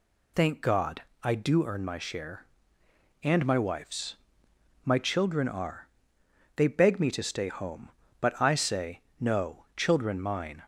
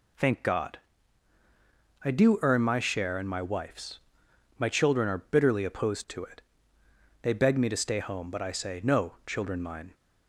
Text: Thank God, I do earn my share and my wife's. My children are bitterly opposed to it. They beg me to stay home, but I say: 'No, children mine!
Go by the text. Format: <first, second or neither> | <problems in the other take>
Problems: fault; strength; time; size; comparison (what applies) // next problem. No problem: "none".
second | skips "bitterly opposed to it"; at 6.2 s